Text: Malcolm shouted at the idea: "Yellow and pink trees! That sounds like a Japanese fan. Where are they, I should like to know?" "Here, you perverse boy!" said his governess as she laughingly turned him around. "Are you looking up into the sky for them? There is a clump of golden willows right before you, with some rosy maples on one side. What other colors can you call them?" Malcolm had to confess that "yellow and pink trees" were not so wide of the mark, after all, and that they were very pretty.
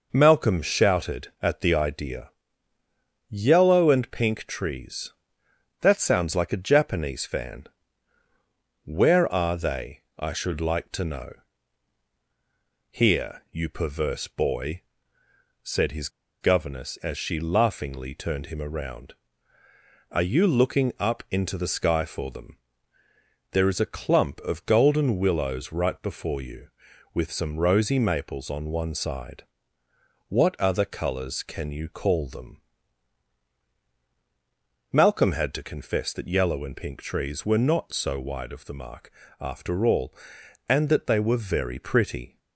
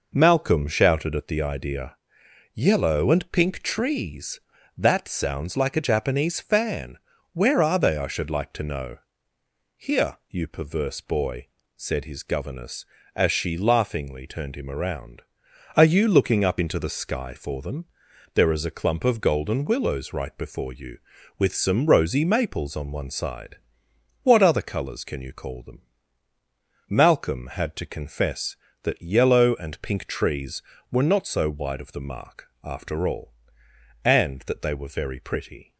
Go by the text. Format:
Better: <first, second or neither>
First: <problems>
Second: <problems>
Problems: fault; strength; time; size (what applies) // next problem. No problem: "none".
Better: second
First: pauses between "his" and "governess"; slight; at 16.0 s; 0.32 s long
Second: none